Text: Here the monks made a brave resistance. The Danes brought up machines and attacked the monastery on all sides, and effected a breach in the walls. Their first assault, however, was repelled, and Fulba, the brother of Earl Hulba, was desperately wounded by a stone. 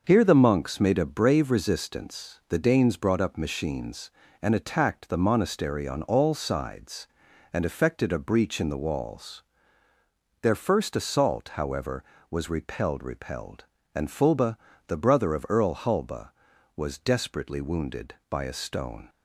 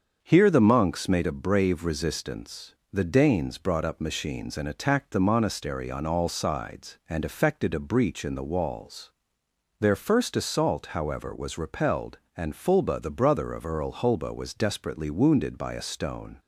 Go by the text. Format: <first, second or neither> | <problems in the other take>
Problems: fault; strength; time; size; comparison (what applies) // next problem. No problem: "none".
second | starts louder than the rest; noticeable; until 1.0 s; 6 dB; also in the second // says "repelled" twice; at 13.0 s